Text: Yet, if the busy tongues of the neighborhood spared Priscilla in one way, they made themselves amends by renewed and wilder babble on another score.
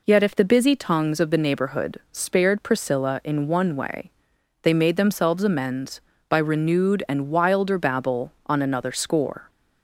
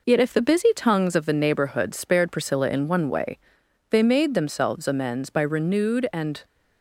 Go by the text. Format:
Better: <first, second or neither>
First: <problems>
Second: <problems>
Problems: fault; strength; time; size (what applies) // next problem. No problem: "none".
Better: first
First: none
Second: stops before "wilder babble on another score"; at 6.4 s